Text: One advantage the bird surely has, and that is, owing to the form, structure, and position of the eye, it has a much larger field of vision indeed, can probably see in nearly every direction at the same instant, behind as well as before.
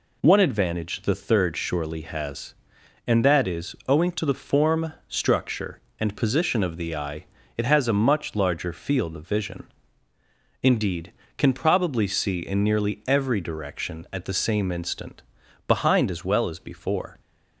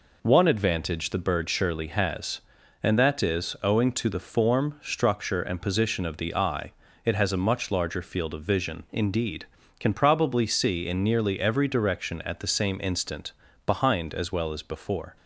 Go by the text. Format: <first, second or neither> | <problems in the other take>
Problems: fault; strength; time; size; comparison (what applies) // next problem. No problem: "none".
second | says "third" for "bird"; at 1.1 s // pauses between "vision" and "indeed"; noticeable; at 9.6 s; 0.96 s long